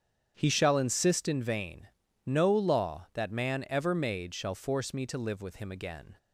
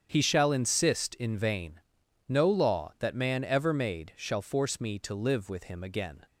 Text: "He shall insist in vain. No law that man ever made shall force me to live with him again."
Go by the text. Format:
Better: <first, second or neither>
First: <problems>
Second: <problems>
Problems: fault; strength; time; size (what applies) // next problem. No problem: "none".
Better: neither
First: starts louder than the rest; strong; until 1.3 s; 8.5 dB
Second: starts louder than the rest; strong; until 1.1 s; 8 dB